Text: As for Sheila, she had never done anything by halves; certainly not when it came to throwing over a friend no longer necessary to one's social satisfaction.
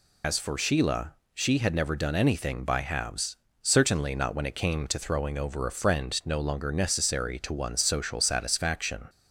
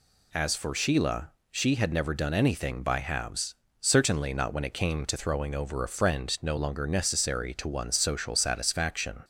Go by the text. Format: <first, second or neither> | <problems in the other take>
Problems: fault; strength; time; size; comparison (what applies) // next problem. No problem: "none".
second | loses the start of "As"; at 0.2 s; 85 ms